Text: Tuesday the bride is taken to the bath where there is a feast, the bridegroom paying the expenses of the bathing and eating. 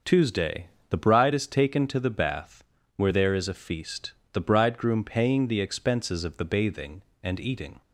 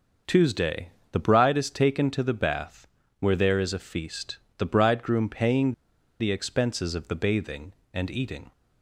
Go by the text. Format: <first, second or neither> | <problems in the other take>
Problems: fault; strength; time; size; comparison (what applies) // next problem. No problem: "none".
first | starts louder than the rest; until 1.5 s; 6.5 dB; also in the first // pauses between "Tuesday" and "the"; slight; at 0.8 s; 0.24 s long; slight in the first // pauses between "bath" and "where"; slight; at 2.8 s; 0.32 s long; slight in the first // pauses between "paying" and "the"; noticeable; at 5.7 s; 0.47 s long